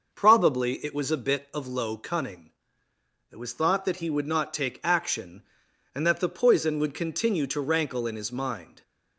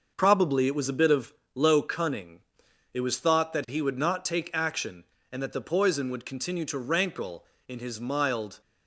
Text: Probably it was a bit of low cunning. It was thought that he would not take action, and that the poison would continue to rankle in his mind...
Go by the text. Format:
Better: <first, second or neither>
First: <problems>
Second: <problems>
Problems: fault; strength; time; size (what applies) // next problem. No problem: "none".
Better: first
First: none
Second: starts louder than the rest; noticeable; until 1.1 s; 6 dB // pauses between "of" and "low"; slight; at 1.3 s; 0.22 s long // says "mild" for "mind"; at 8.0 s